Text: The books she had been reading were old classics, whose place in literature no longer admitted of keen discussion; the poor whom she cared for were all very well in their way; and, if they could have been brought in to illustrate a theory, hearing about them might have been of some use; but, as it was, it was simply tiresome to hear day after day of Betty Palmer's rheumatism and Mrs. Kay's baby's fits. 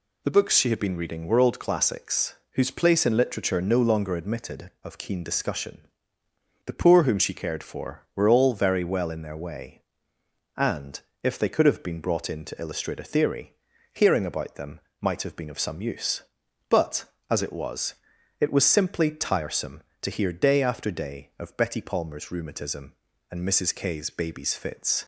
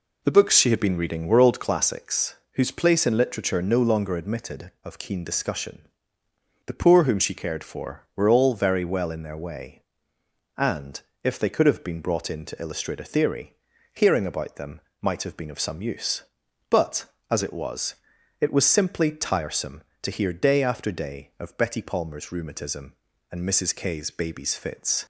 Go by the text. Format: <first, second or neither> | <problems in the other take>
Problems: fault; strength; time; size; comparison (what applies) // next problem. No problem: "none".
first | starts louder than the rest; until 1.8 s; 3.5 dB // pauses between "them" and "might"; slight; at 14.8 s; 0.20 s long; slight in the first